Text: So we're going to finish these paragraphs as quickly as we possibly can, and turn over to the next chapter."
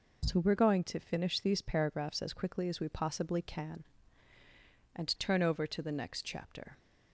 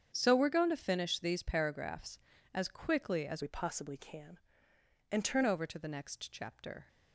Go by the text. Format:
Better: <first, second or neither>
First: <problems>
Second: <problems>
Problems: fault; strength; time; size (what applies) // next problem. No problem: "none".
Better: first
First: none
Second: starts louder than the rest; strong; until 1.1 s; 8 dB // changes voice from "we" to "turn"; from 3.4 to 5.4 s; 2.0 s long